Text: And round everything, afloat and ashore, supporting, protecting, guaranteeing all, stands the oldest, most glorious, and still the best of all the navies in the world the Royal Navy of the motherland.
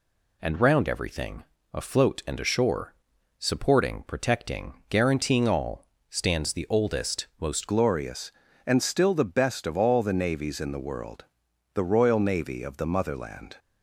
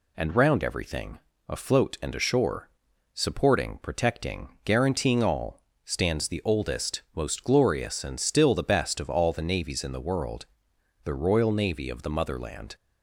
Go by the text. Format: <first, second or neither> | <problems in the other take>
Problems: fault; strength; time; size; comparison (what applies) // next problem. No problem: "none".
second | changes voice at "glorious"; from 7.6 s on; 5.9 s long // pauses between "world" and "the"; noticeable; at 11.2 s; 0.50 s long; noticeable in the second